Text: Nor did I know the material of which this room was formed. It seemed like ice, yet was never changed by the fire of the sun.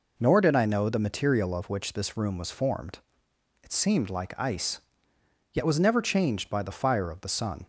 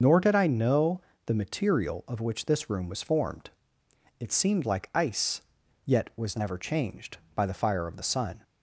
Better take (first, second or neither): first